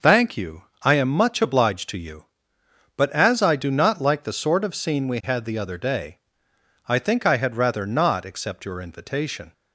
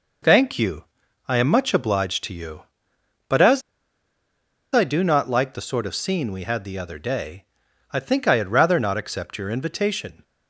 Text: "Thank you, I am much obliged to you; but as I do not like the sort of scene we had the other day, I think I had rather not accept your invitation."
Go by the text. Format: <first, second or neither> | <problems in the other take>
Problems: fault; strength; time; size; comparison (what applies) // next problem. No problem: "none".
first | pauses between "as" and "I"; at 3.6 s; 1.1 s long